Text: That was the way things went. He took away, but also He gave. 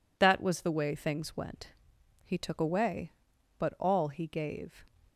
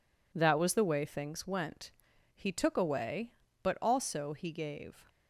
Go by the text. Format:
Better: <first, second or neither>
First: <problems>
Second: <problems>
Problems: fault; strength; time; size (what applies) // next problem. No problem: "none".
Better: second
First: says "all" for "also"; at 3.7 s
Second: none